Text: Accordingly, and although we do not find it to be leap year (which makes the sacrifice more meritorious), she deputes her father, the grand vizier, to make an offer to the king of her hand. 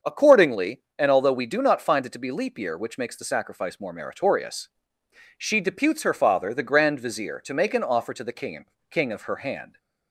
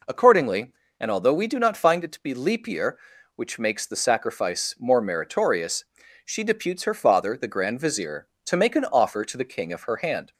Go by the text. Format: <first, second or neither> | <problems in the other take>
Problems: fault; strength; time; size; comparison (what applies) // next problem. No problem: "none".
second | starts louder than the rest; until 1.1 s; 6.5 dB // says "king" twice; at 8.8 s